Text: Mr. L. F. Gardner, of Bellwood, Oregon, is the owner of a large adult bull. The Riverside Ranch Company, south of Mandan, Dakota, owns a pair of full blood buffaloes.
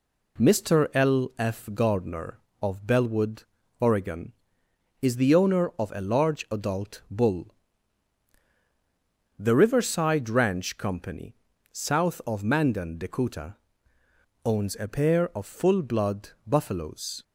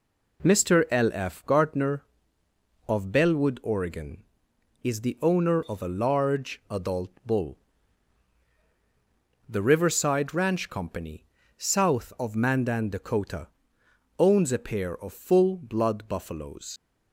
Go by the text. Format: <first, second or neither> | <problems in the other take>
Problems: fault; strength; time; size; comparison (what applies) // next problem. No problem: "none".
first | pauses between "adult" and "bull"; slight; at 7.1 s; 0.16 s long // leaves "buffaloes" unfinished; at 16.7 s; 80 ms